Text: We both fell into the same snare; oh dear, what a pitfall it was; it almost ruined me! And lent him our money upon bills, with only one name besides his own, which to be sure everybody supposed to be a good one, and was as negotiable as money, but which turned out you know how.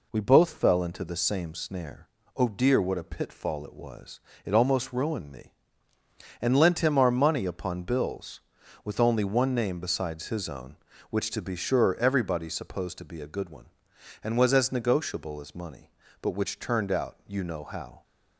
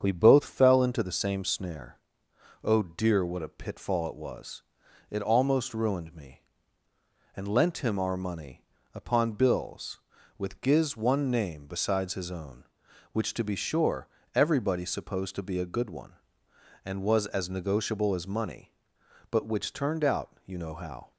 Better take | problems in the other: first | starts louder than the rest; strong; until 1.0 s; 7.5 dB // pauses between "money" and "upon"; slight; at 8.6 s; 0.32 s long // says "giz" for "only"; at 10.5 s // pauses between "sure" and "everybody"; slight; at 14.0 s; 0.26 s long

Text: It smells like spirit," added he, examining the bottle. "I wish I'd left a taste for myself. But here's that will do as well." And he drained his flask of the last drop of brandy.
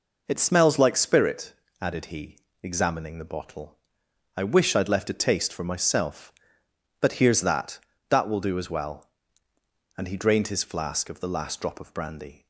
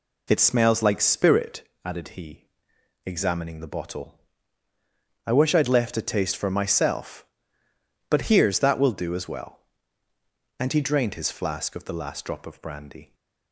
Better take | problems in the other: second | says "that" twice; at 8.0 s

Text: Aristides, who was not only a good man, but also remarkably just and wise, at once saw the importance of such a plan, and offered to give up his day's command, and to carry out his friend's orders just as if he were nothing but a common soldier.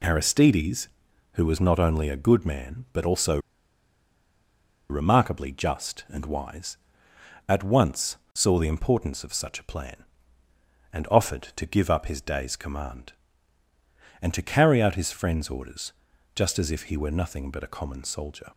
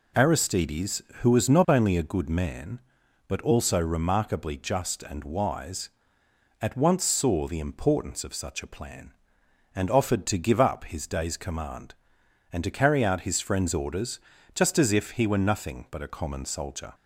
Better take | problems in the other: second | pauses between "also" and "remarkably"; strong; at 3.3 s; 1.5 s long // pauses between "once" and "saw"; slight; at 8.1 s; 0.18 s long // pauses between "orders" and "just"; at 15.9 s; 0.44 s long; slight in the second

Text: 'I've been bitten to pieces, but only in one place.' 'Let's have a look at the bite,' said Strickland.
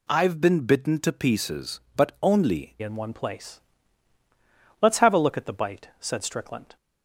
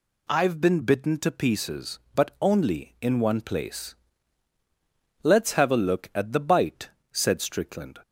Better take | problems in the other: second | changes voice at "in"; from 2.8 s on; 3.9 s long

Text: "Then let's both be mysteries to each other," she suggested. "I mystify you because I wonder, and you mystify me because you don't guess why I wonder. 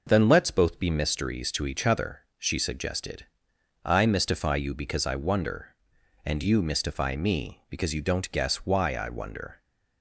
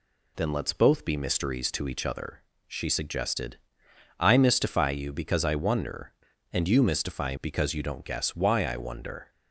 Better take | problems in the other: first | skips "me"; at 7.3 s

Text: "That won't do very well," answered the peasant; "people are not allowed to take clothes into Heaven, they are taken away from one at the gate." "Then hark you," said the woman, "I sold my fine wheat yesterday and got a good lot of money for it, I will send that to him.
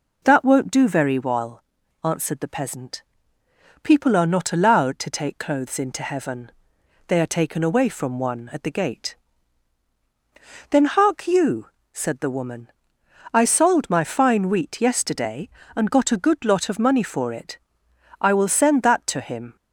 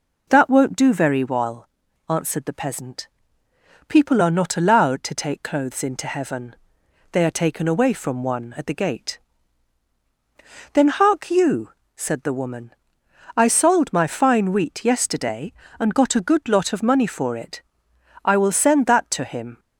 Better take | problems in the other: neither | none

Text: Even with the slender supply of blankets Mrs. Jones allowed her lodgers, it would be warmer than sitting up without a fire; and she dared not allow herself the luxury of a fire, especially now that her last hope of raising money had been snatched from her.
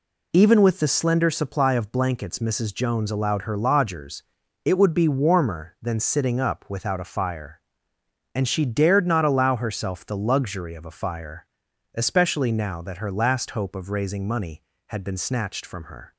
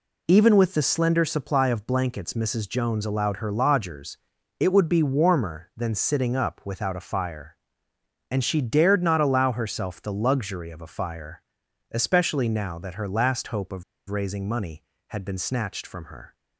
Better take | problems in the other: first | pauses between "of" and "raising"; slight; at 13.8 s; 0.26 s long

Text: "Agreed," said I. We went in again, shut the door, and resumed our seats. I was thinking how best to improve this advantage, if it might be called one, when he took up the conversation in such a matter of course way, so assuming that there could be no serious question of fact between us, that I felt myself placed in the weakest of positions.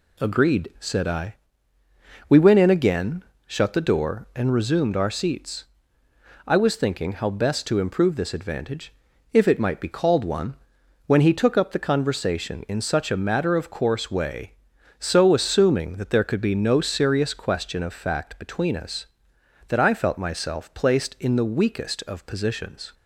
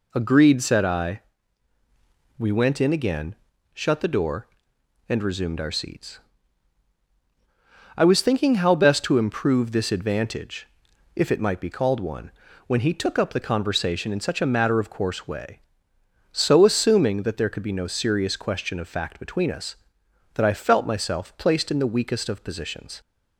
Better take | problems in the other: neither | none

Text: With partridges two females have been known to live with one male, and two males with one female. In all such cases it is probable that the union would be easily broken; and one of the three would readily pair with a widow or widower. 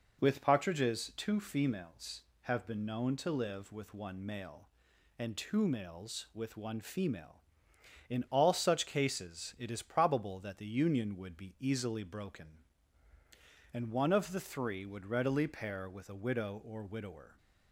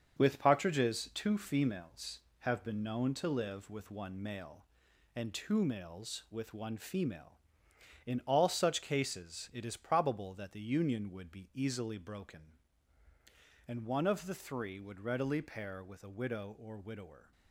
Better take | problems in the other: first | gets quieter; throughout; 6.5 dB

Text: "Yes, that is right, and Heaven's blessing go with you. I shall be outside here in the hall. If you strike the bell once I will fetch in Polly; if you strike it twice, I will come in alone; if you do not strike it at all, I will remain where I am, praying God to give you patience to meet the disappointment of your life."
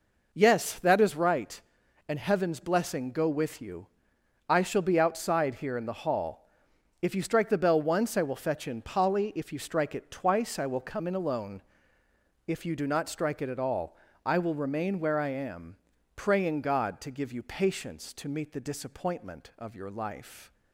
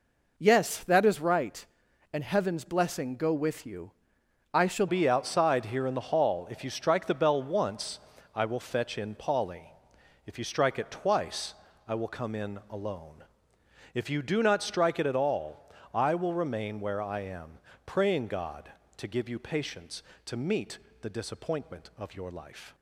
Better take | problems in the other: first | changes voice at "be"; from 4.8 s on; 17.9 s long // pauses between "once" and "I"; slight; at 7.9 s; 0.36 s long // pauses between "meet" and "the"; slight; at 20.7 s; 0.22 s long

